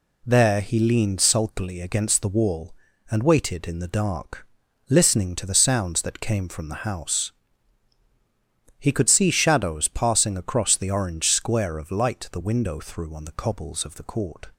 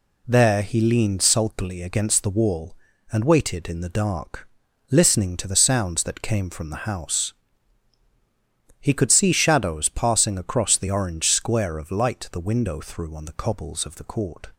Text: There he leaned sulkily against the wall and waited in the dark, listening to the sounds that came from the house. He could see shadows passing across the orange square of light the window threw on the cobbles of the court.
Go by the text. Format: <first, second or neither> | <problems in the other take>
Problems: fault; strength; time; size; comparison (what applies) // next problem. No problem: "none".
neither | none